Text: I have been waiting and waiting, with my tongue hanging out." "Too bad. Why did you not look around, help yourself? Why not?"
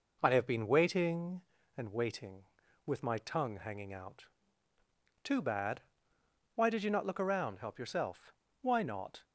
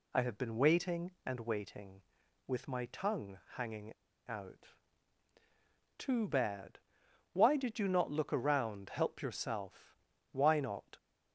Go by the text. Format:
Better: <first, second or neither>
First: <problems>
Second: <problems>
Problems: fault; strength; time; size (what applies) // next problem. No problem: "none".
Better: first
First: none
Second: pauses between "tongue" and "hanging"; slight; at 3.3 s; 0.20 s long // pauses between "hanging" and "out"; slight; at 3.9 s; 0.32 s long